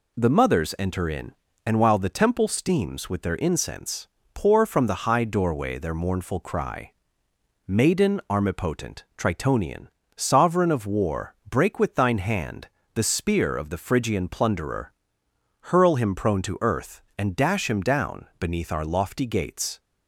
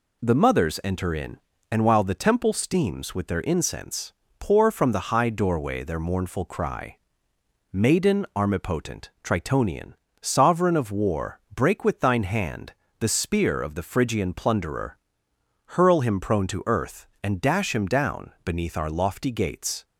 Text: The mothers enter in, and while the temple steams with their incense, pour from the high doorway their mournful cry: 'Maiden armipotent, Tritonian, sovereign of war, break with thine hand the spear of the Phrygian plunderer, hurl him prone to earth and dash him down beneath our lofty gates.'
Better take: neither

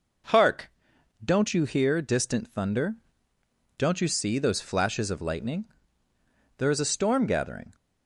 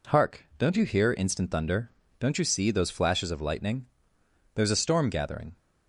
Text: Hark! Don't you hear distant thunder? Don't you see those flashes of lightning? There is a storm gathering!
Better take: first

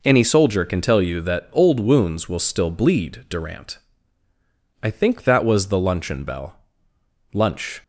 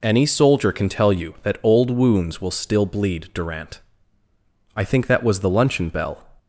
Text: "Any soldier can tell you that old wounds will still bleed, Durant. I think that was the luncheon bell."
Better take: second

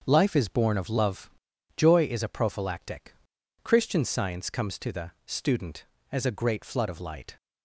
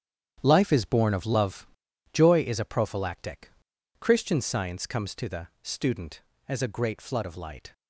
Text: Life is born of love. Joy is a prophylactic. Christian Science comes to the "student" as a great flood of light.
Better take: first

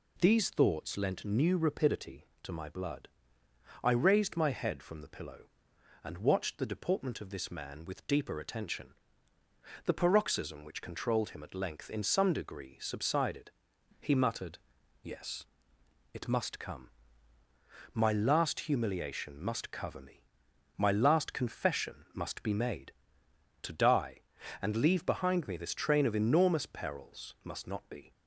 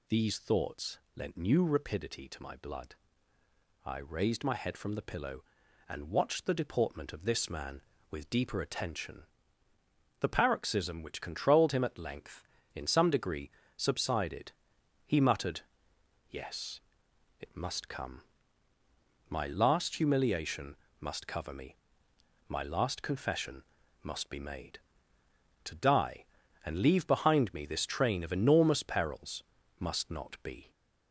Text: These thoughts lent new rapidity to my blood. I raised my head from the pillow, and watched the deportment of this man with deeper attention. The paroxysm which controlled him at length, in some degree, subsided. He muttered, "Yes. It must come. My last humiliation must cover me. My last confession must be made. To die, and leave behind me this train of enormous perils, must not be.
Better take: first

